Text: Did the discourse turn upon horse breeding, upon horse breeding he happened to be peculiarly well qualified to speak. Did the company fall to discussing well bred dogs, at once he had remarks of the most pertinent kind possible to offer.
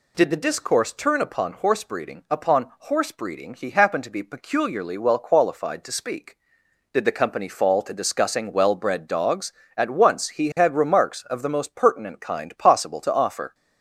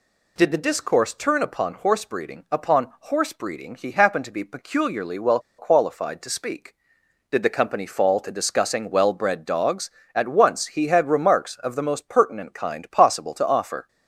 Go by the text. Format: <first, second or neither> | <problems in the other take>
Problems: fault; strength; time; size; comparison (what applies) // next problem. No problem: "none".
first | pauses between "well" and "qualified"; slight; at 5.3 s; 0.19 s long